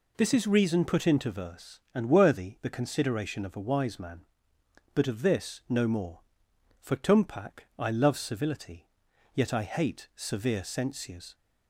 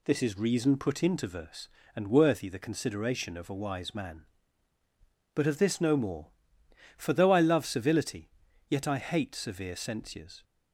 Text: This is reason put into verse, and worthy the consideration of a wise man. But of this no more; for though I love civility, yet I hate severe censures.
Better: second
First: says "tumpak" for "though"; at 6.9 s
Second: none

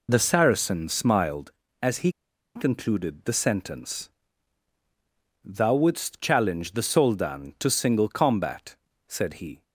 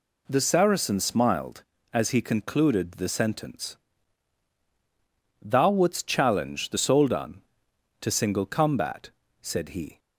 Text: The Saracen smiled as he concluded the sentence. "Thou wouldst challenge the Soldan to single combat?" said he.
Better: second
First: pauses between "he" and "concluded"; at 2.0 s; 0.45 s long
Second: none

